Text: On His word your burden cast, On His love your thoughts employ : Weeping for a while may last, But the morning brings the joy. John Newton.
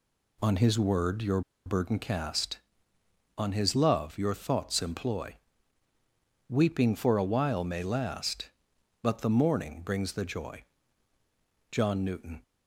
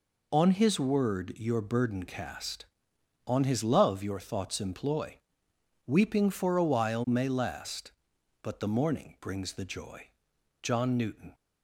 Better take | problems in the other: second | pauses between "your" and "burden"; slight; at 1.4 s; 0.24 s long

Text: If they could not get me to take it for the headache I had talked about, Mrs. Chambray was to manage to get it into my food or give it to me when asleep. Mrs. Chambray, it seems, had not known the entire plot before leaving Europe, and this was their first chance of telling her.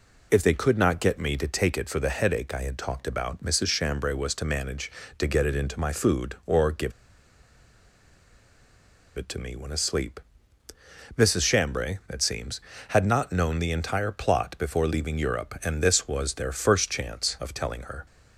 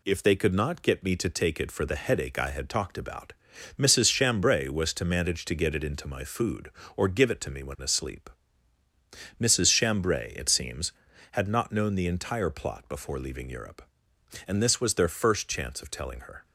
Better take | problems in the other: second | pauses between "give" and "it"; strong; at 6.9 s; 2.2 s long

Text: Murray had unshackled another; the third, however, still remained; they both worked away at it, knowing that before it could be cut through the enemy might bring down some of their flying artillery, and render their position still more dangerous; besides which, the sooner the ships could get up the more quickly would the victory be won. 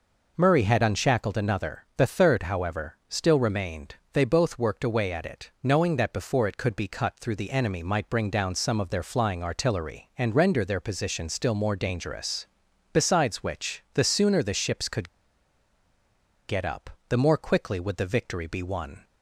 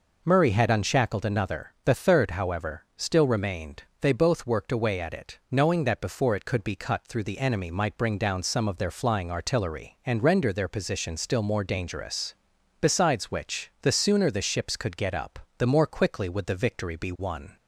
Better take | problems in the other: second | pauses between "could" and "get"; strong; at 15.0 s; 1.3 s long // pauses between "up" and "the"; slight; at 16.8 s; 0.18 s long; slight in the second

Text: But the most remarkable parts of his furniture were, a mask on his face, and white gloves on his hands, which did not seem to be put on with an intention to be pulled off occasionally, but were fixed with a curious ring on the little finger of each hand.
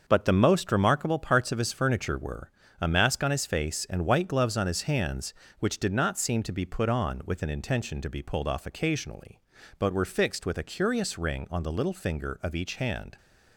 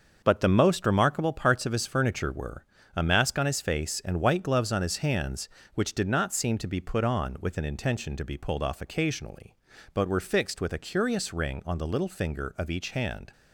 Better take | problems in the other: neither | starts louder than the rest; the same in both

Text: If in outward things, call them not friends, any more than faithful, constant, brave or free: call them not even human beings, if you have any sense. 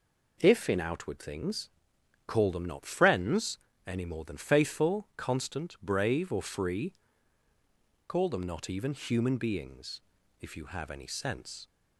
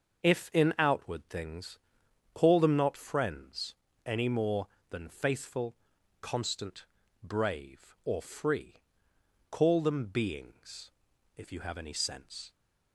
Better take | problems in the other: first | starts louder than the rest; noticeable; until 1.2 s; 6 dB // skips "not even human"; at 10.0 s

